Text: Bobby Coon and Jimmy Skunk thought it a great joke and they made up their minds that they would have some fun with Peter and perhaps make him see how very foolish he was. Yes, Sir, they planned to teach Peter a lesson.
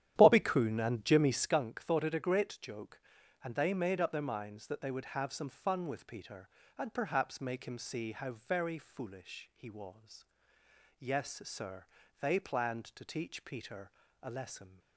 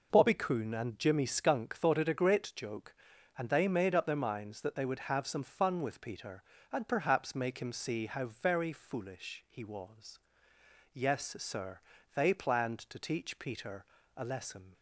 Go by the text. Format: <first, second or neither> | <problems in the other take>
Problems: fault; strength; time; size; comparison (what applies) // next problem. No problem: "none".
second | starts louder than the rest; strong; until 1.6 s; 11 dB // pauses between "Peter" and "a"; slight; at 13.9 s; 0.32 s long; slight in the second